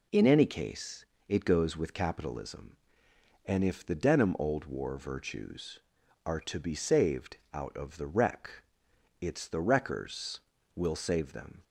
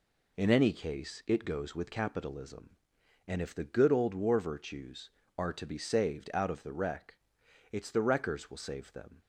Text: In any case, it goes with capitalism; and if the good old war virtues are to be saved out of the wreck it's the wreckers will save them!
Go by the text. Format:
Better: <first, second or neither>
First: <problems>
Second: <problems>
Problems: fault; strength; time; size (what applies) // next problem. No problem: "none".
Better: second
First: says "denim" for "good"; at 3.9 s // pauses between "saved" and "out"; slight; at 7.3 s; 0.18 s long // pauses between "wreck" and "it's"; noticeable; at 8.6 s; 0.56 s long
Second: pauses between "wreck" and "it's"; noticeable; at 7.1 s; 0.58 s long